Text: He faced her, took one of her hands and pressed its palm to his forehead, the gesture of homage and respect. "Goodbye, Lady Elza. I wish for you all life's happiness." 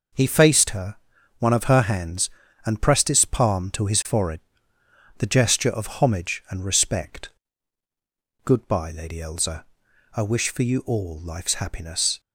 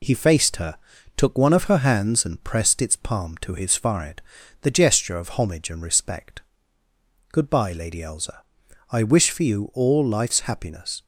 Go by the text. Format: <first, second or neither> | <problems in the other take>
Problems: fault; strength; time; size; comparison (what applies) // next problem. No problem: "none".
second | skips "took"; at 1.1 s